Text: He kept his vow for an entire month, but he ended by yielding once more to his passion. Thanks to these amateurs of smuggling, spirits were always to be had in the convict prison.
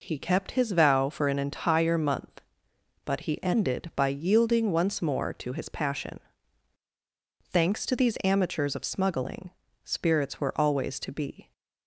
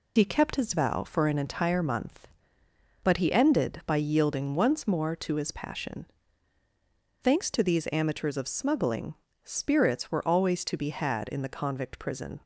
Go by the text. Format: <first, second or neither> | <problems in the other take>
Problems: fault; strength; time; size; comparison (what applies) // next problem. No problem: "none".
second | stops before "had in the convict prison"; at 11.5 s